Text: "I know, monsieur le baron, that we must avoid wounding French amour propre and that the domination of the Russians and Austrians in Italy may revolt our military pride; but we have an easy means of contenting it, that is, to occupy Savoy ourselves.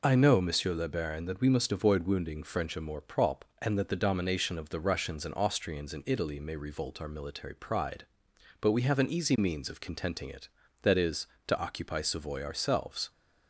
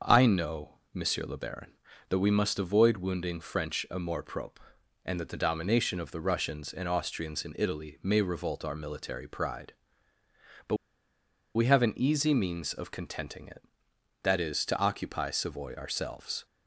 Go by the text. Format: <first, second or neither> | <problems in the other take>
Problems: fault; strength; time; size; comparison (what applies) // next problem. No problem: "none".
first | starts louder than the rest; until 1.1 s; 6.5 dB // pauses between "but" and "we"; noticeable; at 10.7 s; 0.80 s long